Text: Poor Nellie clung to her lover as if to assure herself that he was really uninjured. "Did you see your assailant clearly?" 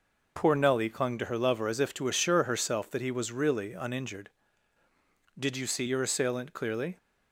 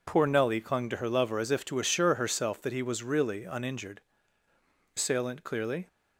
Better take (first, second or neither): first